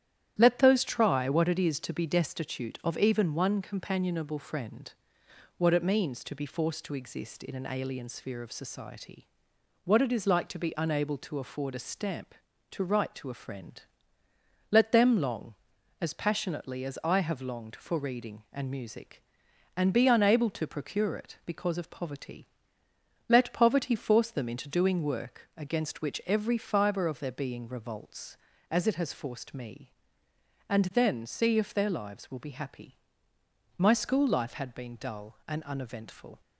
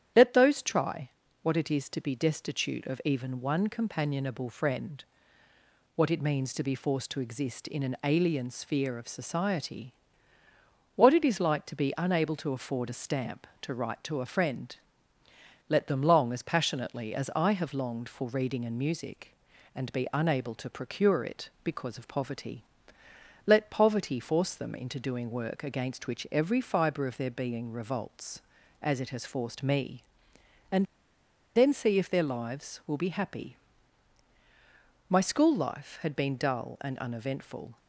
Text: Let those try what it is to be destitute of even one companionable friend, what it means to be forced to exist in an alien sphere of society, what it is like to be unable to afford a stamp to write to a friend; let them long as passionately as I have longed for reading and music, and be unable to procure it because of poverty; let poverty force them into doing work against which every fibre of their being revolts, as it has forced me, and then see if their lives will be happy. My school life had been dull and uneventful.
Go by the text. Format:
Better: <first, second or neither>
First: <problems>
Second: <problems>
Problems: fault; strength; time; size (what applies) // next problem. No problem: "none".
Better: first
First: starts louder than the rest; strong; until 1.3 s; 11 dB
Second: starts louder than the rest; strong; until 1.4 s; 10 dB // pauses between "try" and "what"; slight; at 1.0 s; 0.32 s long // pauses between "and" and "then"; noticeable; at 30.8 s; 0.72 s long